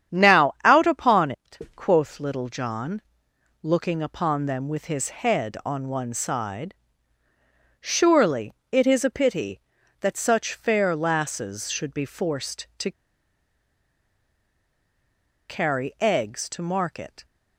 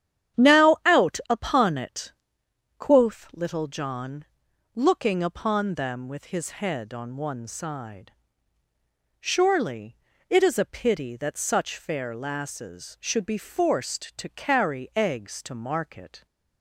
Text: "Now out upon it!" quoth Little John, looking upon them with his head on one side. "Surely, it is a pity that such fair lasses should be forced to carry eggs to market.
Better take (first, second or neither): second